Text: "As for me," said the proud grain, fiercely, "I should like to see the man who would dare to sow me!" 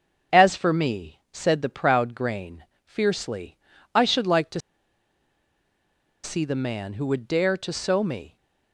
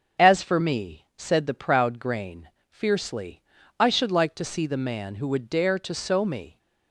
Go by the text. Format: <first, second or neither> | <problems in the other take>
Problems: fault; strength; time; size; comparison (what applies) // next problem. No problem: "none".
second | starts louder than the rest; until 1.4 s; 6.5 dB; also in the second // pauses between "to" and "see"; strong; at 4.5 s; 1.6 s long